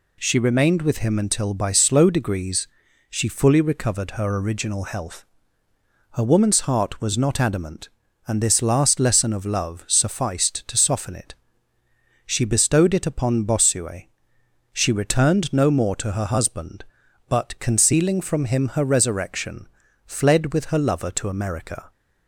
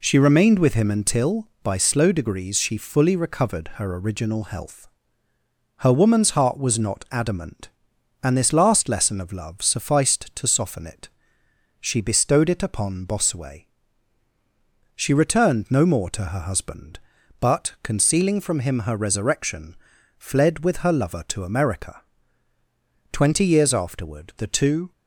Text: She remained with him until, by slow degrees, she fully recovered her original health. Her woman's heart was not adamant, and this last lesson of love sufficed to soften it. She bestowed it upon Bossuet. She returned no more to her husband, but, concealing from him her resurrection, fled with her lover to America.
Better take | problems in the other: first | goes on to say "Twenty years afterward the two"; strong; from 23.1 s on; 1.8 s long

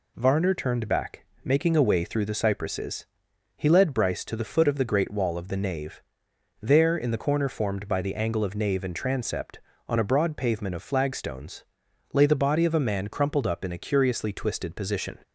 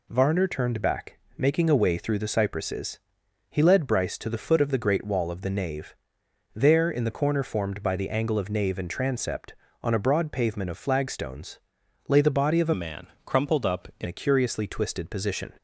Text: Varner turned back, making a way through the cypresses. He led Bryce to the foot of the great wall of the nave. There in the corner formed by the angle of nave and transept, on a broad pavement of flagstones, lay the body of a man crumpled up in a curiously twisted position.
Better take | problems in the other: first | changes voice from "man" to "in"; from 12.7 to 14.0 s; 1.3 s long // pauses between "man" and "crumpled"; slight; at 13.0 s; 0.18 s long

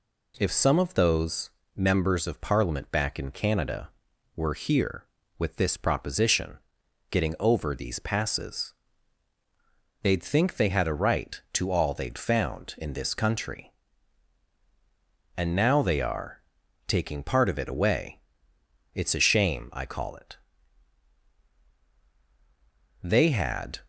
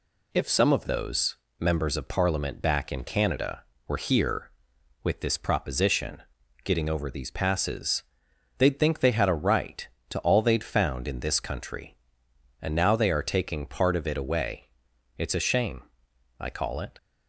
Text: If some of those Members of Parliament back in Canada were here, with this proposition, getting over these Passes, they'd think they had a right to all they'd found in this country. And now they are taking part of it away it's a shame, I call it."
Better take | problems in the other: second | pauses between "those" and "Members"; slight; at 1.4 s; 0.28 s long; slight in the second // pauses between "are" and "taking"; noticeable; at 16.4 s; 0.46 s long // pauses between "away" and "it's"; noticeable; at 18.1 s; 0.74 s long; noticeable in the second // goes on to say "They had"; noticeable; from 23.0 s on; 0.76 s long

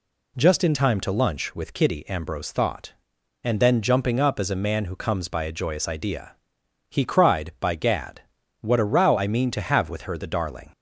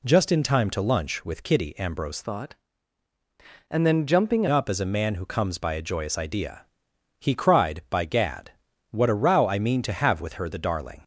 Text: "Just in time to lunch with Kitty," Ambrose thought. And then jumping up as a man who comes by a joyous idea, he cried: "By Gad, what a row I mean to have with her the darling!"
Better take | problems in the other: first | changes voice from "thought" to "jumping"; from 2.2 to 4.4 s; 2.2 s long

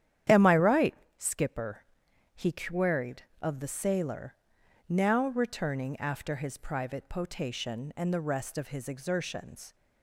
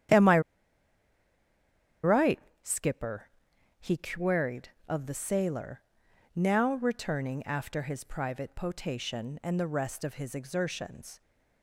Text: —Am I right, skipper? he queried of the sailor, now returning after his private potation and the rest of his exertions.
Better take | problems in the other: first | starts louder than the rest; strong; until 3.0 s; 10 dB; strong in the first // pauses between "I" and "right"; strong; at 0.4 s; 1.6 s long

